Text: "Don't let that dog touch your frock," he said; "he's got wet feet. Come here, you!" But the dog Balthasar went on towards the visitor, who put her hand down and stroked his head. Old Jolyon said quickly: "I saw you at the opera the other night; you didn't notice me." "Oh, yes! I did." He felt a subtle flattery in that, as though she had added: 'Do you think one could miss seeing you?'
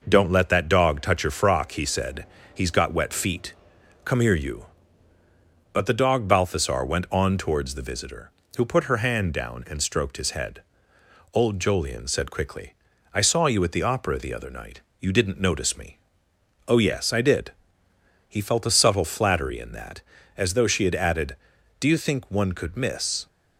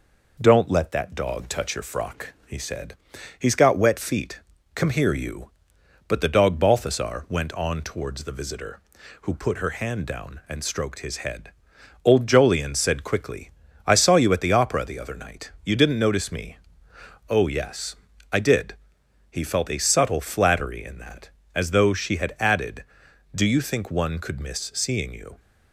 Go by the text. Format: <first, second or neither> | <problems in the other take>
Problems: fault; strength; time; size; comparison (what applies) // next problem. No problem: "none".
second | stops before "seeing you"; at 23.2 s